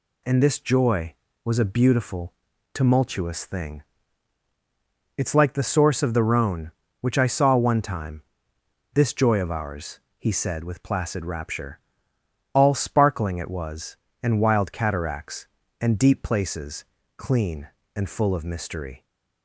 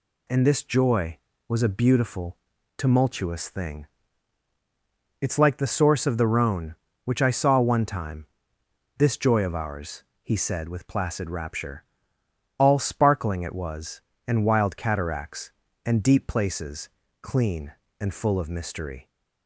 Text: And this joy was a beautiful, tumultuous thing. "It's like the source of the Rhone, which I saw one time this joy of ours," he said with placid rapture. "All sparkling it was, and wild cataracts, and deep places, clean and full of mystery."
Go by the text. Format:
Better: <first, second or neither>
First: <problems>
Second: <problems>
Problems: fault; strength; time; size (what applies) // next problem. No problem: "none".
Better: neither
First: pauses between "time" and "this"; noticeable; at 8.2 s; 0.70 s long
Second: pauses between "time" and "this"; noticeable; at 8.2 s; 0.70 s long